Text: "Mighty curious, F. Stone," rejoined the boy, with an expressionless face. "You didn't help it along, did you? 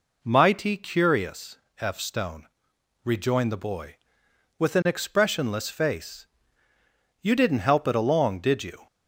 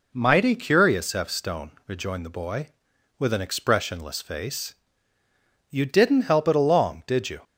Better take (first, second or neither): neither